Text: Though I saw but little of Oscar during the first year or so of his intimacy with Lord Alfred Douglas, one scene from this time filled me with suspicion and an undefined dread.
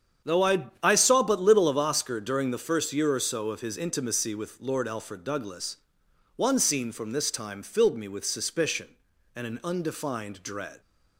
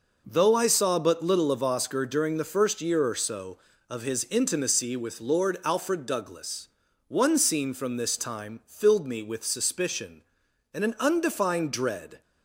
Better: second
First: starts louder than the rest; strong; until 1.4 s; 8 dB // says "I" twice; at 0.8 s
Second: none

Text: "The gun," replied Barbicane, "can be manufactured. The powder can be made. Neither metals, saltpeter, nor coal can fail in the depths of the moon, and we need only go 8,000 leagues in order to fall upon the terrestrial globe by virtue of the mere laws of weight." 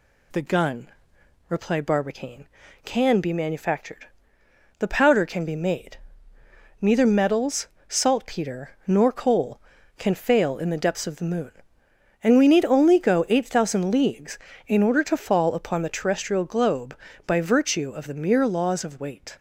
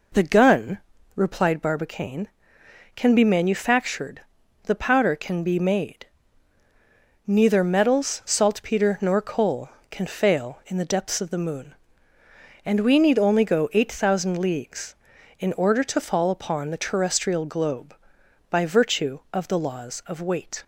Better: first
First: none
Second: skips "mere"; at 19.5 s

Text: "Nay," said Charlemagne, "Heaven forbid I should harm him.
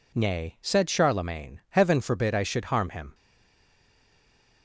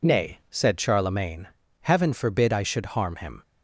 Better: second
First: stays silent after the last word; noticeable; from 3.1 s on; 1.5 s long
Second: none

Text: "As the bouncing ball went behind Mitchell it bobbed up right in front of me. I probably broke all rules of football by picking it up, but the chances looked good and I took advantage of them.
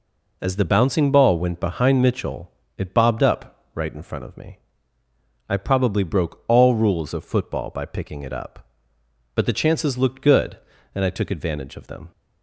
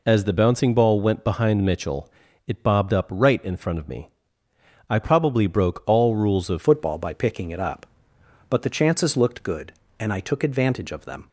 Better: first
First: pauses between "Mitchell" and "it"; slight; at 2.4 s; 0.28 s long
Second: pauses between "Mitchell" and "it"; at 2.0 s; 0.38 s long // changes voice at "football"; from 6.6 s on; 4.6 s long

